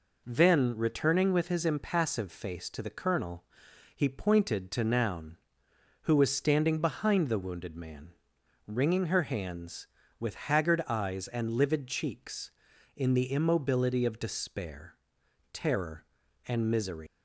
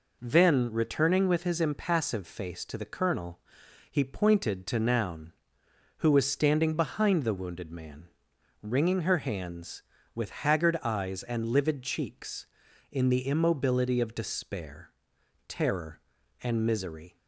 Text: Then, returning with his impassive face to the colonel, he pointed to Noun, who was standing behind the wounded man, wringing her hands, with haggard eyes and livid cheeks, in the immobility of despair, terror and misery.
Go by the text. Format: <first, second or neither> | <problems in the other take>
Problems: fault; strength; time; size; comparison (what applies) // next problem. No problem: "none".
second | leaves "misery" unfinished; at 17.0 s; 150 ms